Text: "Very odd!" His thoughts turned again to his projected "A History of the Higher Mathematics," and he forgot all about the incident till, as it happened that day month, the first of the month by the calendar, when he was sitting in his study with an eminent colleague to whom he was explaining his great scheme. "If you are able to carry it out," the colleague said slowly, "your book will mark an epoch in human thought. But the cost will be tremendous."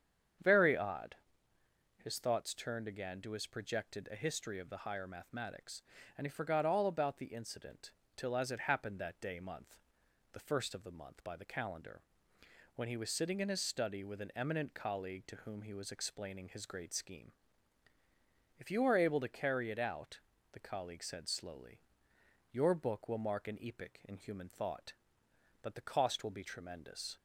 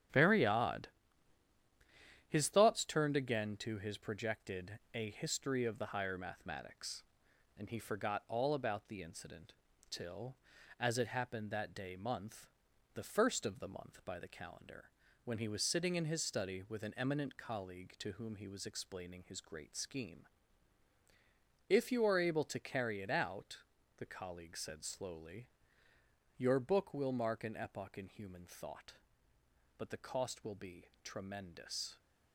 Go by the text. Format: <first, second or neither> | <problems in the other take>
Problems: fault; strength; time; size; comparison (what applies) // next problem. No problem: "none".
first | gets quieter; strong; throughout; 7 dB // starts louder than the rest; strong; until 2.5 s; 9 dB; strong in the first // pauses between "incident" and "till"; slight; at 9.5 s; 0.36 s long; slight in the first